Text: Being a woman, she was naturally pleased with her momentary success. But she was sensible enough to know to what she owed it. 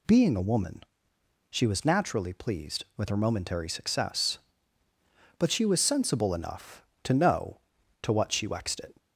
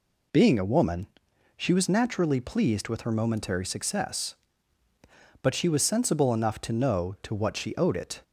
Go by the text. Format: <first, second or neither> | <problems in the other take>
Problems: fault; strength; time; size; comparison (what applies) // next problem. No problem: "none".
second | says "wexed" for "owed"; at 8.4 s